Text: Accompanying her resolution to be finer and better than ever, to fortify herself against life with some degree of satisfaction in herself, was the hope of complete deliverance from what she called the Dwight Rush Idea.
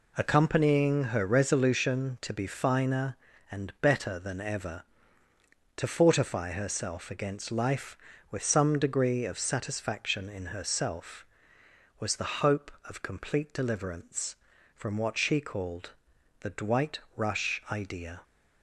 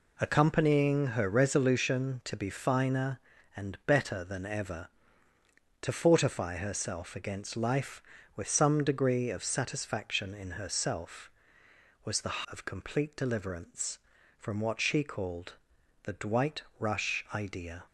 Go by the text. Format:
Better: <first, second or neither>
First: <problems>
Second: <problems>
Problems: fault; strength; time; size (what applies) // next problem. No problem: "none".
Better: first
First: pauses between "called" and "the"; noticeable; at 15.9 s; 0.50 s long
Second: skips "hope"; at 12.4 s // pauses between "called" and "the"; noticeable; at 15.5 s; 0.50 s long